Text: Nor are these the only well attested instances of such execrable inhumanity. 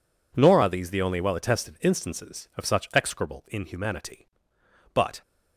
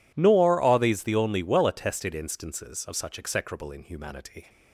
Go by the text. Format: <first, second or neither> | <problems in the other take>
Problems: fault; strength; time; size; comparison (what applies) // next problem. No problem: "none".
second | goes on to say "But"; slight; from 4.9 s on; 0.28 s long